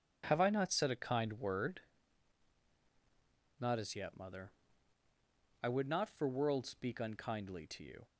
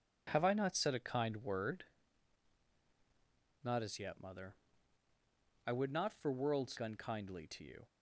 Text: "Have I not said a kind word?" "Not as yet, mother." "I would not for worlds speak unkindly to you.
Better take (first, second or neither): first